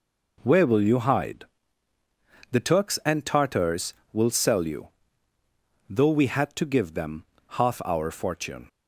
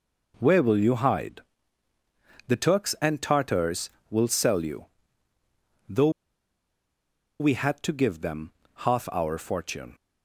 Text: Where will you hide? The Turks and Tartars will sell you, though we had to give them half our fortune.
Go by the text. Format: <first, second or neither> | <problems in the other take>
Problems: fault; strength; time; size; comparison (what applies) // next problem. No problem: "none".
first | pauses between "though" and "we"; strong; at 6.0 s; 1.3 s long // pauses between "them" and "half"; slight; at 8.5 s; 0.24 s long; slight in the first